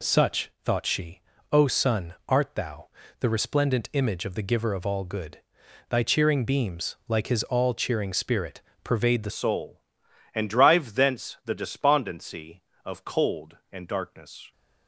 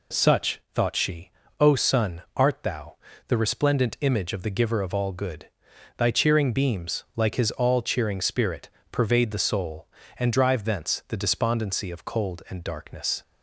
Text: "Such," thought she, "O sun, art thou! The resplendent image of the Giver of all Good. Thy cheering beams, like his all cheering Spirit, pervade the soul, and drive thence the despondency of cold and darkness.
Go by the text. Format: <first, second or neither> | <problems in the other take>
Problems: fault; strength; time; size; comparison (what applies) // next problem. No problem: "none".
second | changes voice at "soul"; from 9.3 s on; 5.2 s long